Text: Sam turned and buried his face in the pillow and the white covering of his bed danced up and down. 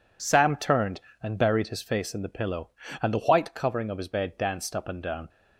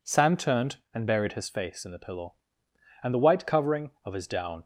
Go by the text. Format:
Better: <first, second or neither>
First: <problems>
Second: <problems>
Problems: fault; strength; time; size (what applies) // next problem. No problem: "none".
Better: first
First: none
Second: skips "bed danced up and"; at 4.2 s